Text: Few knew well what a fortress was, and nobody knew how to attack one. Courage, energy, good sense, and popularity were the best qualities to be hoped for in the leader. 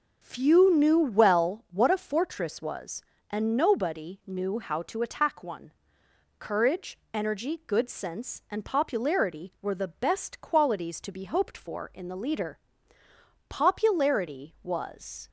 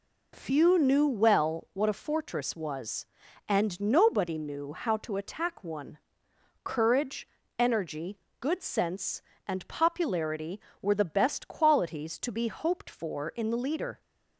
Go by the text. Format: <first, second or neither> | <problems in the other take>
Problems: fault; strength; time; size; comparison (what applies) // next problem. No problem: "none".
second | goes on to say "Popularity was"; strong; from 13.4 s on; 1.8 s long